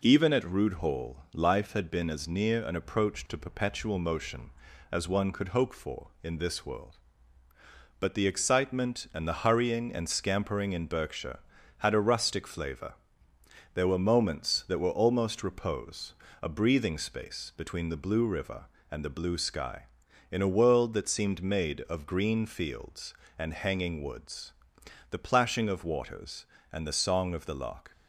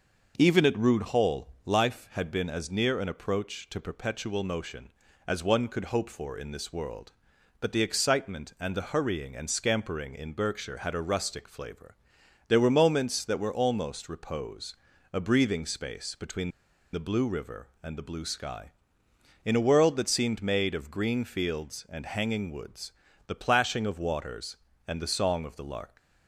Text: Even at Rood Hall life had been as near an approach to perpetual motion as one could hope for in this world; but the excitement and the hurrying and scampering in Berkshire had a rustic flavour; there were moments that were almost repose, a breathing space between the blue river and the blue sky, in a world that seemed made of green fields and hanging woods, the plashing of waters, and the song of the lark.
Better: first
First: none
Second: starts louder than the rest; noticeable; until 1.3 s; 6 dB // pauses between "Hall" and "life"; slight; at 1.4 s; 0.16 s long // pauses between "between" and "the"; at 16.4 s; 0.43 s long

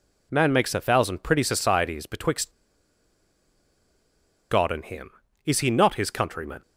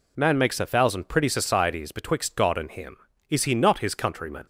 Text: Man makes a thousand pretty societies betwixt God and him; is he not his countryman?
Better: second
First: pauses between "betwixt" and "God"; strong; at 2.4 s; 2.0 s long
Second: none

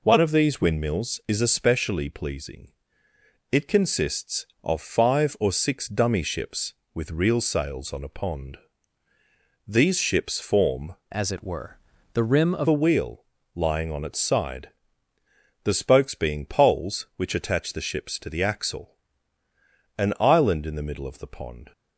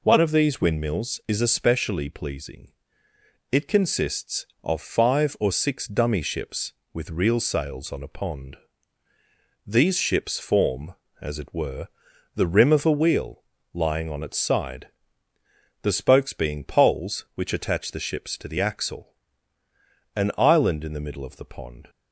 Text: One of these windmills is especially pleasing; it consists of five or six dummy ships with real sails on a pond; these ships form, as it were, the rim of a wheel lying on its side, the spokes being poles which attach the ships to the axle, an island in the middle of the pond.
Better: second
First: changes voice from "as" to "of"; from 11.1 to 12.6 s; 1.5 s long // pauses between "wheel" and "lying"; slight; at 13.2 s; 0.28 s long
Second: pauses between "wheel" and "lying"; slight; at 13.4 s; 0.28 s long

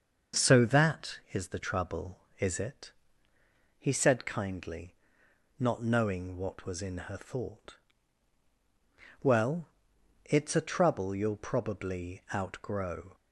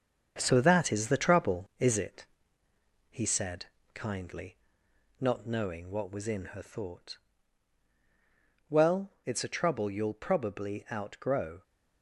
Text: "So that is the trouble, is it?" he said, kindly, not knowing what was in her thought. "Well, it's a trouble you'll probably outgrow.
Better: first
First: starts louder than the rest; until 1.4 s; 6.5 dB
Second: gets quieter; noticeable; throughout; 6 dB // starts louder than the rest; strong; until 1.3 s; 7 dB

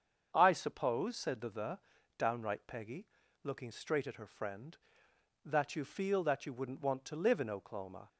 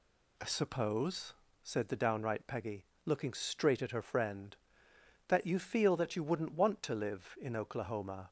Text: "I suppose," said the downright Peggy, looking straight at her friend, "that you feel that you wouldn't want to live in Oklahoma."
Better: second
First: starts louder than the rest; strong; until 1.3 s; 7.5 dB // says "the" twice; at 1.4 s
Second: none

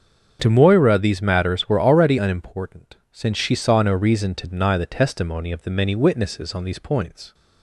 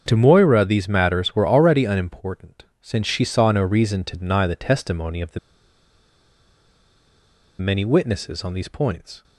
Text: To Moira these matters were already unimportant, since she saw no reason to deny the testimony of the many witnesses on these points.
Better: first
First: starts louder than the rest; until 1.4 s; 7 dB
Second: starts louder than the rest; until 1.0 s; 7 dB // pauses between "the" and "many"; strong; at 5.3 s; 2.2 s long

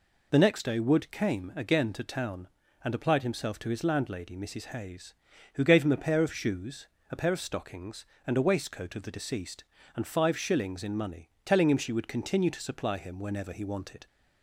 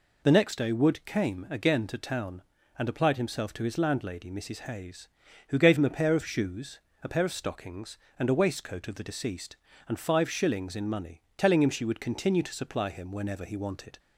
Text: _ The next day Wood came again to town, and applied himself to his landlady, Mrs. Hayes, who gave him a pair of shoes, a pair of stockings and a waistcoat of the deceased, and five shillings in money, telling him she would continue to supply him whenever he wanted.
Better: neither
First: none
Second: none

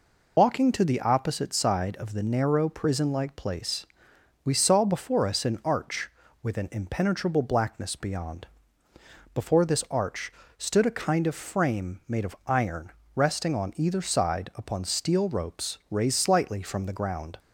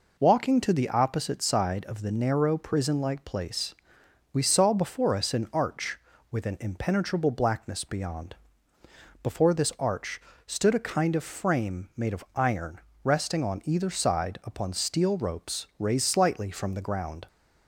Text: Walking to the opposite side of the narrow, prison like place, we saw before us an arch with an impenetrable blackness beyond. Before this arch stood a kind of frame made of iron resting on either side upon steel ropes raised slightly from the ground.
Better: second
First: loses the start of "Walking"; at 0.3 s; 65 ms // pauses between "arch" and "stood"; slight; at 10.3 s; 0.28 s long // pauses between "iron" and "resting"; slight; at 12.9 s; 0.24 s long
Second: pauses between "arch" and "stood"; slight; at 10.1 s; 0.28 s long // pauses between "iron" and "resting"; slight; at 12.7 s; 0.24 s long

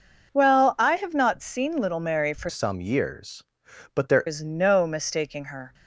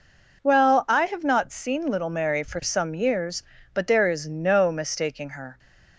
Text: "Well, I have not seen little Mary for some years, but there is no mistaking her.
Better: second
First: changes voice from "some" to "there"; from 2.4 to 4.2 s; 1.8 s long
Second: none

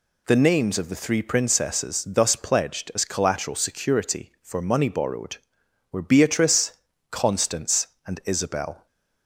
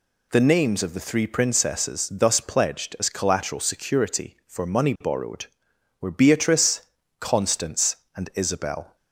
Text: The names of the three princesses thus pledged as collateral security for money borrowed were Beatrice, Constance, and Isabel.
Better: neither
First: none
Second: none

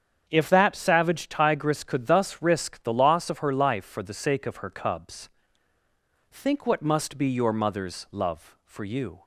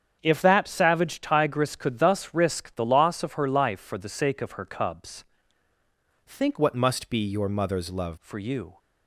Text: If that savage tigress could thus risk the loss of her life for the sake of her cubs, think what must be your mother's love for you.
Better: first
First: starts louder than the rest; strong; until 1.2 s; 8 dB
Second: starts louder than the rest; strong; until 1.2 s; 8 dB // changes voice from "what" to "love"; from 6.5 to 8.1 s; 1.6 s long

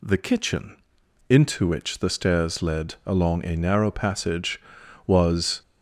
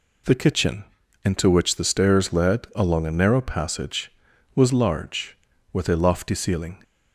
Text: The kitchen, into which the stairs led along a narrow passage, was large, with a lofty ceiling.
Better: second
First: stops before "large with a lofty ceiling"; at 5.6 s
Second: none

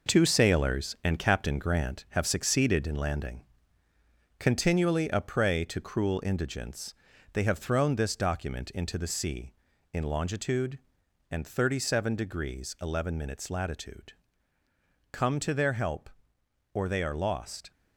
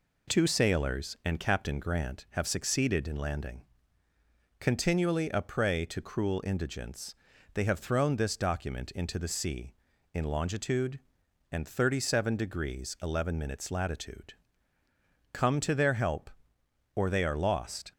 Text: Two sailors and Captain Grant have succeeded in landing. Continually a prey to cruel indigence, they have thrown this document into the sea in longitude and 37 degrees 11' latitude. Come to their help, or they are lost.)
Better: second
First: gets quieter; throughout; 7 dB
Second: none

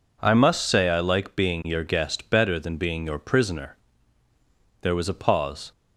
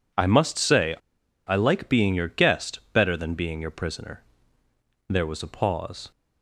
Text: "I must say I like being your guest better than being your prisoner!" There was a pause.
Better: first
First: none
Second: pauses between "say" and "I"; noticeable; at 0.9 s; 0.52 s long

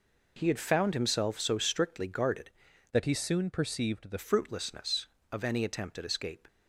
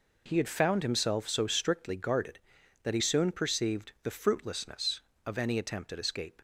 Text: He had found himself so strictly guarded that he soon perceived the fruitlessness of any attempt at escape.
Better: second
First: changes voice from "that" to "the"; from 2.9 to 4.1 s; 1.2 s long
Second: none

